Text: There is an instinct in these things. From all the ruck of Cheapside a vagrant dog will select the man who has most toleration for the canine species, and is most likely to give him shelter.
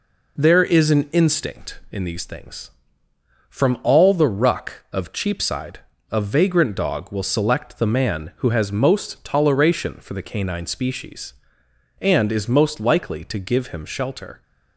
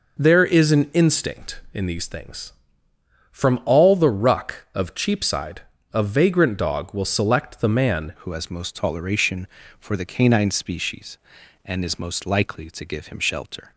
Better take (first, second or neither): first